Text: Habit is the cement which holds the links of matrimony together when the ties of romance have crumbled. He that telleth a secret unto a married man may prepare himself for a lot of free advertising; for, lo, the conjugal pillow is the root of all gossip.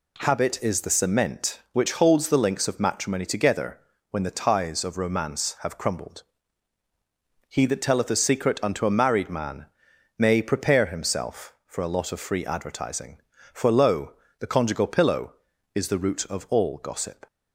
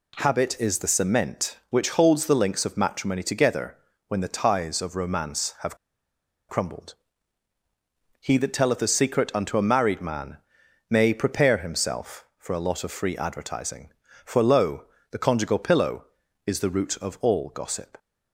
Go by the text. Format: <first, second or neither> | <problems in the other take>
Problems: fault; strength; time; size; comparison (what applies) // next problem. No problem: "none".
first | pauses between "together" and "when"; slight; at 3.7 s; 0.32 s long; slight in the first // pauses between "have" and "crumbled"; noticeable; at 5.7 s; 0.72 s long // pauses between "man" and "may"; noticeable; at 10.3 s; 0.50 s long; noticeable in the first